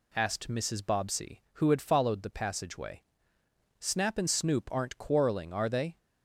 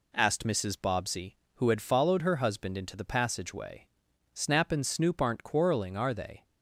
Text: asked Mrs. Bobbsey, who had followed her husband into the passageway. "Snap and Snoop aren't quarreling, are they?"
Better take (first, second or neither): second